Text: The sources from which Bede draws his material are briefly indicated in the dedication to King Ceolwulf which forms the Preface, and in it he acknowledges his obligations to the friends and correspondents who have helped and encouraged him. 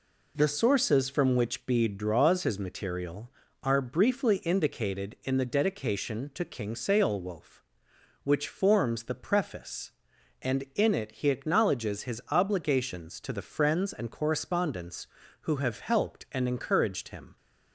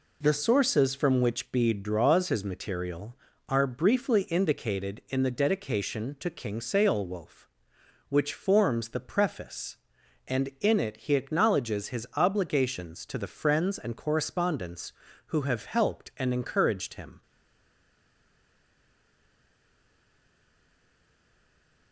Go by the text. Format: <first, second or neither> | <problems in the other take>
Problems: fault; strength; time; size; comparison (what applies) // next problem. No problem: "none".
first | stays silent after the last word; strong; from 17.2 s on; 4.7 s long